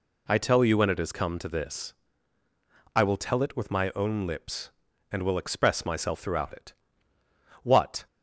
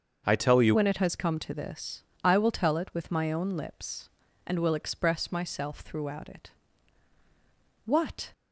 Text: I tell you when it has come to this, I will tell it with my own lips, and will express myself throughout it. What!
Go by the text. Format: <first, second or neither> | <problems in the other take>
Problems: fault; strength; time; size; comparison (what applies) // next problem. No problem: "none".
first | starts louder than the rest; until 1.2 s; 6.5 dB // changes voice at "when"; from 0.7 s on; 7.6 s long